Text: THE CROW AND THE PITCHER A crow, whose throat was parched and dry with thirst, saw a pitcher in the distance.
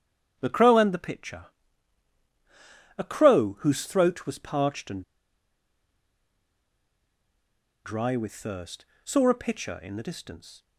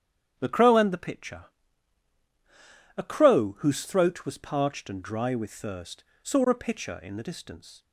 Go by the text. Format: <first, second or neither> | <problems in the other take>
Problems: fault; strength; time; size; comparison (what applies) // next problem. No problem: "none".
second | starts louder than the rest; strong; until 1.4 s; 9 dB; strong in the second // pauses between "PITCHER" and "A"; strong; at 1.4 s; 1.5 s long; strong in the second // pauses between "and" and "dry"; strong; at 5.0 s; 2.8 s long